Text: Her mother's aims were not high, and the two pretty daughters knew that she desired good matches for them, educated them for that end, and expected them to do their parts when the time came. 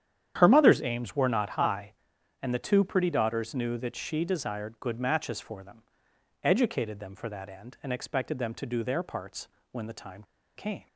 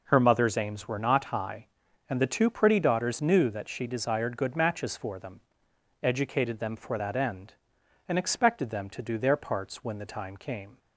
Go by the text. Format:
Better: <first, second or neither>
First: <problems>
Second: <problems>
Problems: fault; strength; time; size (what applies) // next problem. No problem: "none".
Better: second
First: starts louder than the rest; strong; until 1.3 s; 9.5 dB // pauses between "parts" and "when"; slight; at 9.4 s; 0.24 s long // pauses between "time" and "came"; slight; at 10.2 s; 0.33 s long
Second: none